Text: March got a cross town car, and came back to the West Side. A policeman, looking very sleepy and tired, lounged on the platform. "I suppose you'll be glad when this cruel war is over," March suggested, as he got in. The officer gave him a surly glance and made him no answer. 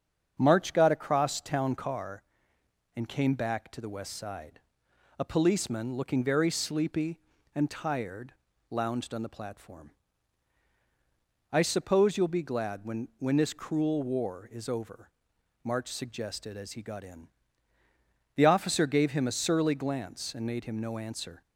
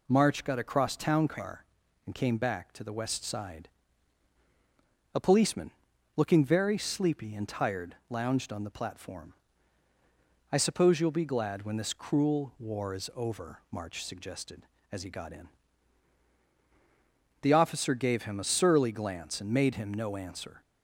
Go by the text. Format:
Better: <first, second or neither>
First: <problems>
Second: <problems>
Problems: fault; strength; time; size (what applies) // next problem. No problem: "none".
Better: second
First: starts louder than the rest; strong; until 1.3 s; 7 dB // says "when" twice; at 13.1 s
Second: none